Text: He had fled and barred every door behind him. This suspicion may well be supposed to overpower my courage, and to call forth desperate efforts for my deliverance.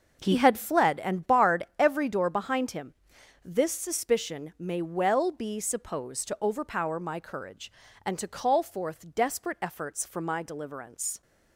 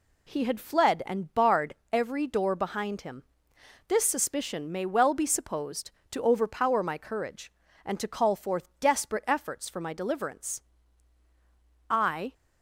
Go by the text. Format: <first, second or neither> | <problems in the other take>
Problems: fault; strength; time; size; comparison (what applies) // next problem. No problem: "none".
first | pauses between "barred" and "every"; slight; at 1.7 s; 0.16 s long // goes on to say "I"; slight; from 11.8 s on; 0.44 s long